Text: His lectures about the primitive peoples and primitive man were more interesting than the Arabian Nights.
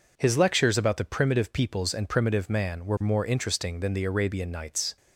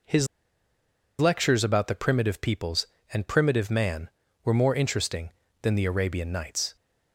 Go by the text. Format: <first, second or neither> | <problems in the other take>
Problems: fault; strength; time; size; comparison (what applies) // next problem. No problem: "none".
first | pauses between "His" and "lectures"; noticeable; at 0.2 s; 0.92 s long